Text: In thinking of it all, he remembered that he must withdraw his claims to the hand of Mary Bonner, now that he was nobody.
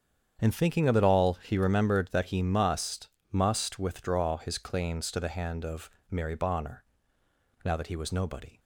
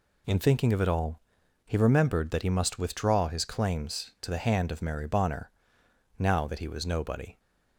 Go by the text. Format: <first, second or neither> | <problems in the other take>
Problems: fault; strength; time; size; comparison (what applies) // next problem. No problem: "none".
second | starts louder than the rest; strong; until 1.4 s; 8 dB // says "must" twice; at 3.3 s // pauses between "of" and "Mary"; slight; at 5.8 s; 0.20 s long